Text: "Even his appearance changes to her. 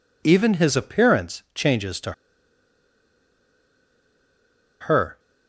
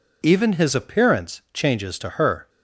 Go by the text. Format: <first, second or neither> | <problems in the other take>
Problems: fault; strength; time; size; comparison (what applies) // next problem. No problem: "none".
second | pauses between "to" and "her"; strong; at 2.1 s; 2.7 s long